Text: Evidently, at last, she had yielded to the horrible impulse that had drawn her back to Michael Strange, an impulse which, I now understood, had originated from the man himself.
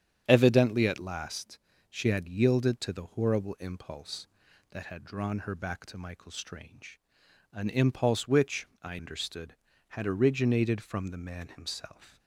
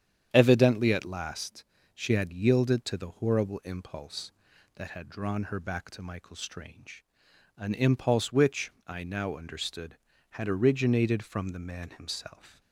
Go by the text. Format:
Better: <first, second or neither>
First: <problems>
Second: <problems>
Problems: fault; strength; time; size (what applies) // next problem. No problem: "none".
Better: second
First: starts louder than the rest; strong; until 1.2 s; 9 dB // skips "now"; at 8.9 s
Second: starts louder than the rest; strong; until 1.3 s; 9 dB